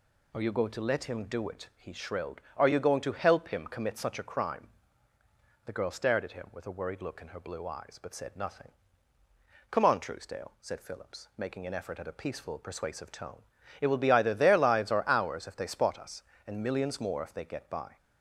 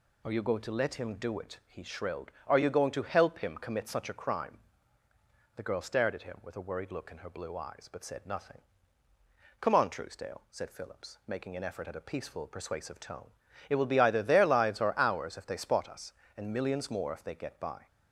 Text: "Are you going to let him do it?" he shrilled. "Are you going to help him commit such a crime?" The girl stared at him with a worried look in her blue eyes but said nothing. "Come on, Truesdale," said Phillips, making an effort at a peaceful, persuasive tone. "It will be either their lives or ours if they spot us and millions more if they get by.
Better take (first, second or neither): neither